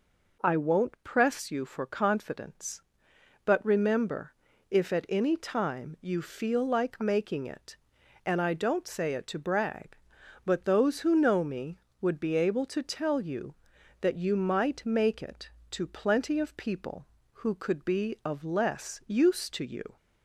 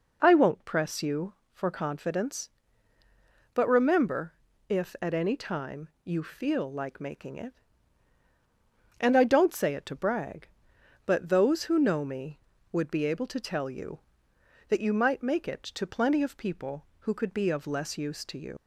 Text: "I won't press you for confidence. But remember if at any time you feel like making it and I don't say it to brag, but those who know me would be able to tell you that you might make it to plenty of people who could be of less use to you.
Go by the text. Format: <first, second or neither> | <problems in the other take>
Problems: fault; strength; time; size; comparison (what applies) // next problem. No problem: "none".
first | pauses between "remember" and "if"; slight; at 4.3 s; 0.36 s long; slight in the first // pauses between "time" and "you"; slight; at 5.8 s; 0.16 s long // leaves "you" unfinished; at 18.5 s; 80 ms